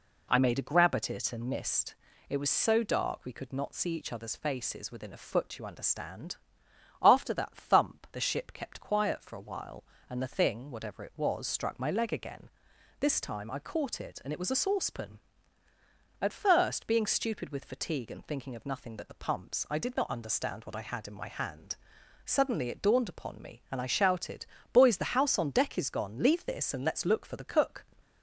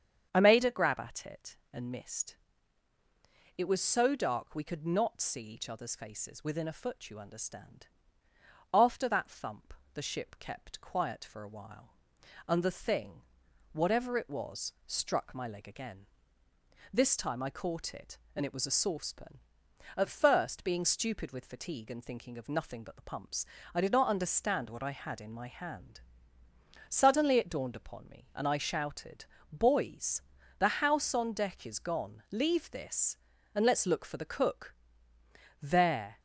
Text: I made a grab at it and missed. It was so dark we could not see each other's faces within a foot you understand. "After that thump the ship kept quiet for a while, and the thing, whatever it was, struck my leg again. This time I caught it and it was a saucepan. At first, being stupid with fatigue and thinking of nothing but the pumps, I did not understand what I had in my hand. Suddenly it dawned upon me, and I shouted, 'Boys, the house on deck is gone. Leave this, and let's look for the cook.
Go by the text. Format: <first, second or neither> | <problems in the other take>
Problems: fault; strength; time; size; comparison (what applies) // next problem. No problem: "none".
first | starts louder than the rest; strong; until 1.3 s; 8 dB // pauses between "thump" and "the"; slight; at 9.7 s; 0.22 s long // goes on to say "There"; from 35.6 s on; 0.58 s long